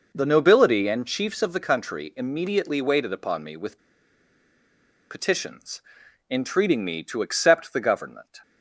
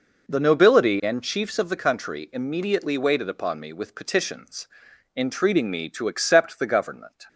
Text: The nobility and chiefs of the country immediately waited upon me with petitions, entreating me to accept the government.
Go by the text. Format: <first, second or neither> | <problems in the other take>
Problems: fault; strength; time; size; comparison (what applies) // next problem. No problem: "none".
second | pauses between "with" and "petitions"; strong; at 3.7 s; 1.3 s long